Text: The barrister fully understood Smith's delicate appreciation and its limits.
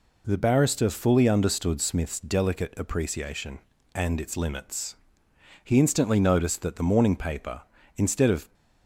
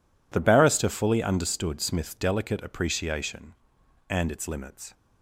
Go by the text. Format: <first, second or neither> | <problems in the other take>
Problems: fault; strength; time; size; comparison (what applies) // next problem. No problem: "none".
second | goes on to say "He instantly noticed that the morning paper instead of"; strong; from 5.6 s on; 2.9 s long